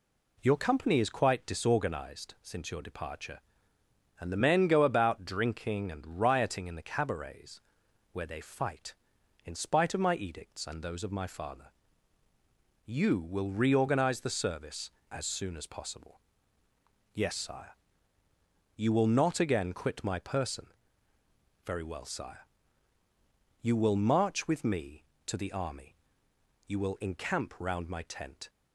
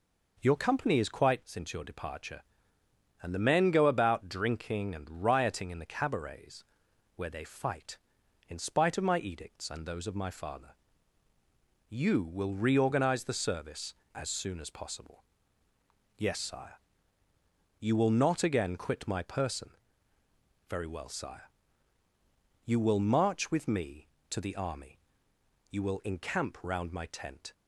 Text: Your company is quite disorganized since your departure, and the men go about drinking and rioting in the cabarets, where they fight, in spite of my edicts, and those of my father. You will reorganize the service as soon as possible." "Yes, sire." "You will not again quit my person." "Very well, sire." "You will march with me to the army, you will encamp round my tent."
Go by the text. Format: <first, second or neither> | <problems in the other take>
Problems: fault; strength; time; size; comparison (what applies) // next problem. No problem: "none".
first | skips "disorganized"; at 1.4 s